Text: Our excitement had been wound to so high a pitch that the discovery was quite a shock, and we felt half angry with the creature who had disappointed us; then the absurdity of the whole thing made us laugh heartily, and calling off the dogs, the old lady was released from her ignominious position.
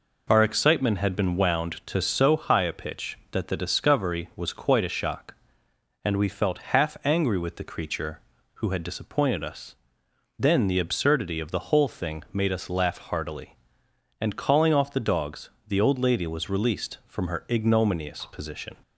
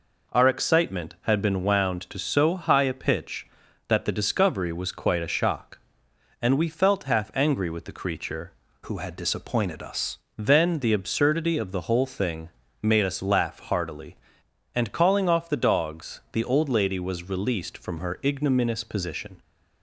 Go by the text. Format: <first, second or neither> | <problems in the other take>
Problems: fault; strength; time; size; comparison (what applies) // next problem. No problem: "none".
first | changes voice from "who" to "us"; from 8.8 to 10.1 s; 1.3 s long // pauses between "thing" and "made"; slight; at 12.4 s; 0.32 s long